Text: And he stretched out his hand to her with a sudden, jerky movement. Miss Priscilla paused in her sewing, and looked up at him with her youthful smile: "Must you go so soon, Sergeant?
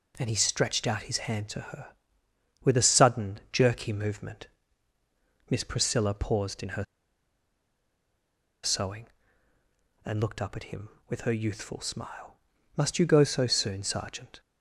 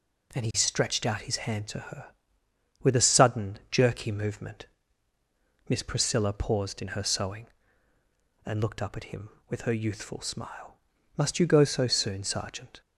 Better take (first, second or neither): second